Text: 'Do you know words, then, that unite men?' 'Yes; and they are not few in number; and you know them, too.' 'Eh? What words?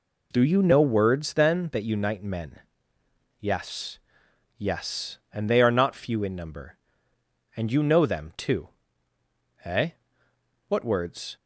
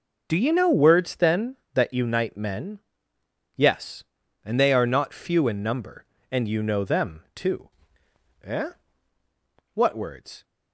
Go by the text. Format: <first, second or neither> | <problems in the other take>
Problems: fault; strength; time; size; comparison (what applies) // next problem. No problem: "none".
second | says "Yes" twice; at 4.5 s